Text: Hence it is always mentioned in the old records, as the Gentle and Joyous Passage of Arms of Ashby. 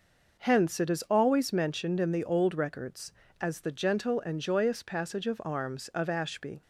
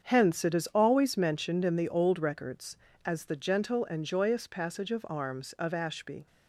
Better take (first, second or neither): first